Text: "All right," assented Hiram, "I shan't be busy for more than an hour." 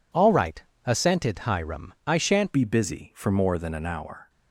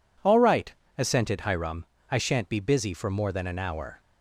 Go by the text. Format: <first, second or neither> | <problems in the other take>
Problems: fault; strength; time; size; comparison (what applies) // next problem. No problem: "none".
second | changes voice at "be"; from 2.5 s on; 1.7 s long